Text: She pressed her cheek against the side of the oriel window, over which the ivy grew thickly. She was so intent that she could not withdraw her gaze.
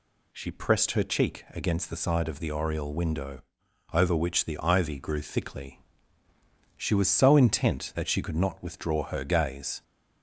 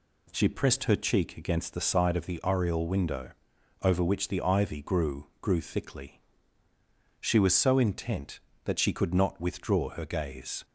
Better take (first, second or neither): first